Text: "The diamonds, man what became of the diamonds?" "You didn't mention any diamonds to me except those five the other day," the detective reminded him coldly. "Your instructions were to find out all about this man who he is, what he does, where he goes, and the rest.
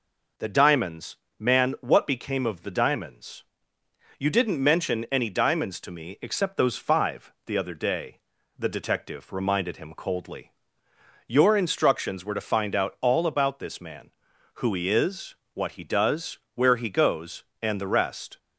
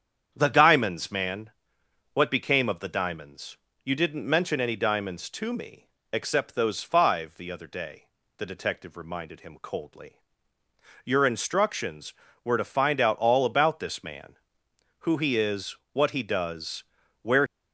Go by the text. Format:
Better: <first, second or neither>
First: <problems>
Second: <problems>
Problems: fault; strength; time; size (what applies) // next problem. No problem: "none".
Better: first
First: none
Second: starts louder than the rest; strong; until 1.3 s; 8 dB // pauses between "man" and "what"; noticeable; at 1.5 s; 0.62 s long // pauses between "me" and "except"; slight; at 5.8 s; 0.24 s long // stops before "he goes and the rest"; at 17.4 s